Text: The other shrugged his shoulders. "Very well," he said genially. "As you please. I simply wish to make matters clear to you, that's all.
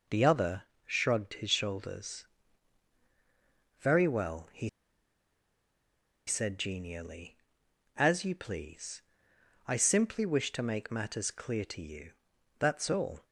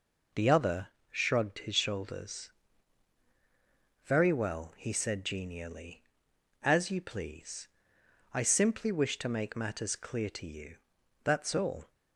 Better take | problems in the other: second | pauses between "other" and "shrugged"; slight; at 0.6 s; 0.22 s long; slight in the second // pauses between "he" and "said"; strong; at 4.6 s; 1.5 s long

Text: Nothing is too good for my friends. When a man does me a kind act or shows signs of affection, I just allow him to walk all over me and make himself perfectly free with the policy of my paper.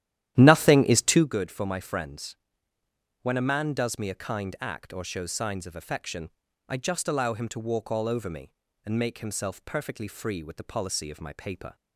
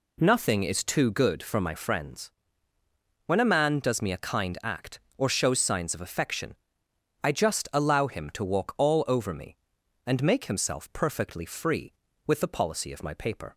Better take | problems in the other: second | starts louder than the rest; strong; until 1.3 s; 12 dB

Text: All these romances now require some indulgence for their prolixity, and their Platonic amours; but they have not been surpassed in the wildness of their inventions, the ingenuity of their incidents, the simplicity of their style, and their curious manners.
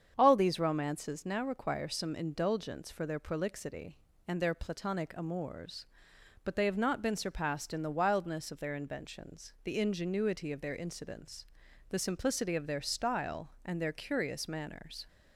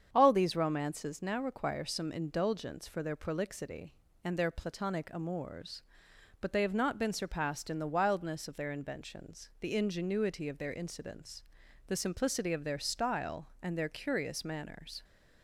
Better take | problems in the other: neither | starts louder than the rest; strong; the same in both

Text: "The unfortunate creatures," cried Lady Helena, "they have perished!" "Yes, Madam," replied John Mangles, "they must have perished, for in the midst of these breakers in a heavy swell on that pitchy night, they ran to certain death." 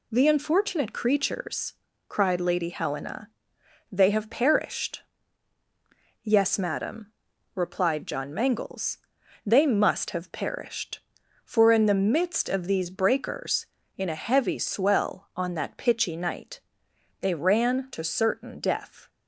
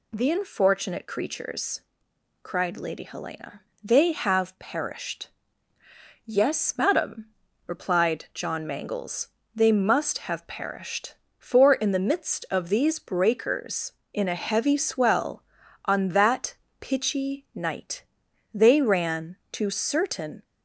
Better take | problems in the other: first | pauses between "that" and "pitchy"; slight; at 16.5 s; 0.26 s long // stops before "death"; at 20.4 s

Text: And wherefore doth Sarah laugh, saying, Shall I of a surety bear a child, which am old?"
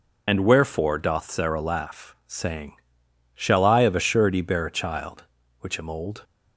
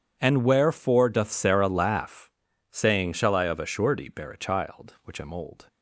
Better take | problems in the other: second | loses the start of "And"; at 0.2 s; 35 ms

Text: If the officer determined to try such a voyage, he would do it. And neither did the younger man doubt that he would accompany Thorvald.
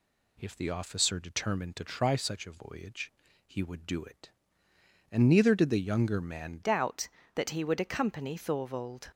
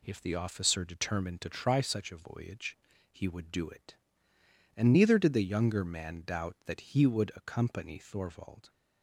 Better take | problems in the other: second | changes voice at "doubt"; from 6.6 s on; 2.4 s long

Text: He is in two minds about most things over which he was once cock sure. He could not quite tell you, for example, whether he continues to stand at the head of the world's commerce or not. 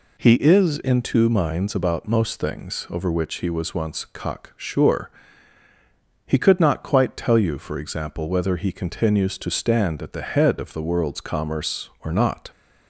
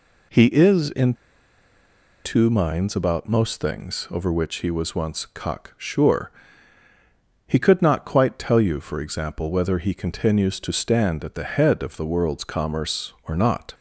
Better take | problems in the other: first | pauses between "in" and "two"; at 1.1 s; 1.0 s long

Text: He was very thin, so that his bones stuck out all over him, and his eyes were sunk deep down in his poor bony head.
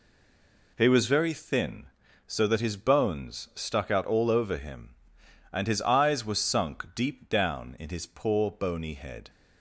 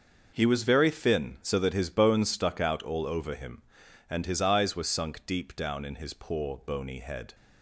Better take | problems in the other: second | stays silent before the first word; slight; until 0.7 s; 0.7 s long

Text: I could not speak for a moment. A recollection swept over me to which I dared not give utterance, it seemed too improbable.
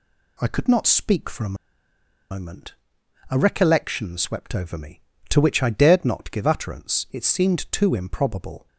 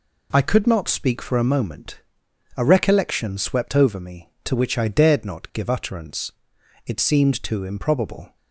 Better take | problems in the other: second | pauses between "a" and "moment"; noticeable; at 1.5 s; 0.74 s long

